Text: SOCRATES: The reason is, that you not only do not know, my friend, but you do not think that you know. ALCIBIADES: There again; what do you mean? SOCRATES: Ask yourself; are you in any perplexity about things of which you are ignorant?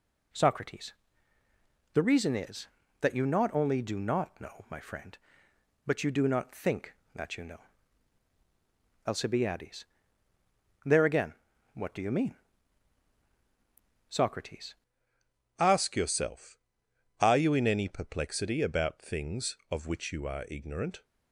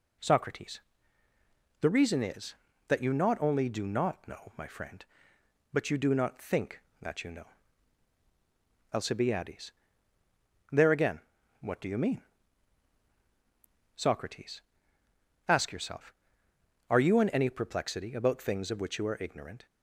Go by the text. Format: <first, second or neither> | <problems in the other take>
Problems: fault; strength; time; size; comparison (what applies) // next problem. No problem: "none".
second | changes voice at "Ask"; from 15.6 s on; 5.4 s long